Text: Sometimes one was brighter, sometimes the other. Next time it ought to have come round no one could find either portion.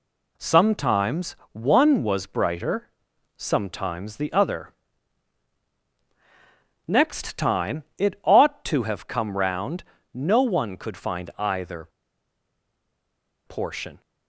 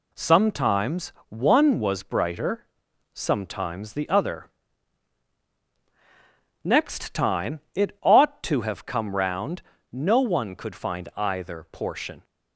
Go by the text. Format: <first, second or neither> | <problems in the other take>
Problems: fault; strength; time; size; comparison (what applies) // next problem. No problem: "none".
second | pauses between "Sometimes" and "one"; slight; at 1.3 s; 0.18 s long; slight in the second // pauses between "round" and "no"; slight; at 9.8 s; 0.34 s long; slight in the second // pauses between "either" and "portion"; strong; at 11.8 s; 1.5 s long